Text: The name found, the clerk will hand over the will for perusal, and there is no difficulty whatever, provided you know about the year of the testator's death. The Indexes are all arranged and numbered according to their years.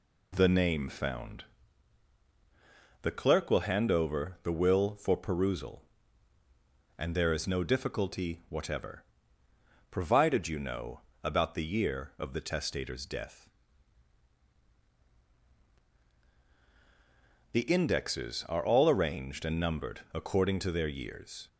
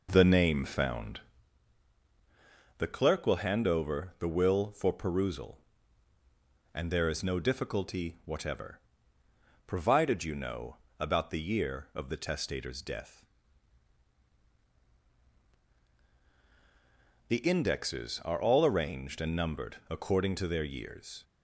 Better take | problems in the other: first | starts louder than the rest; noticeable; until 1.5 s; 5 dB // pauses between "know" and "about"; slight; at 10.7 s; 0.20 s long; slight in the first // pauses between "numbered" and "according"; slight; at 19.7 s; 0.16 s long; slight in the first

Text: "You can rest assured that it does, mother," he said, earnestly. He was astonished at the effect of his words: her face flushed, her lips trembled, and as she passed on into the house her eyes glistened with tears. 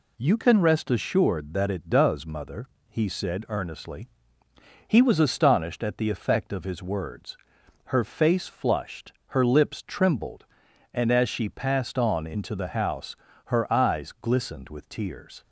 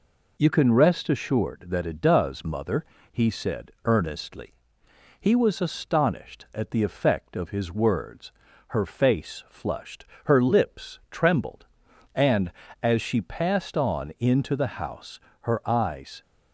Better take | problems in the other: first | pauses between "house" and "her"; slight; at 15.1 s; 0.22 s long; slight in the first // stops before "glistened with tears"; at 16.2 s

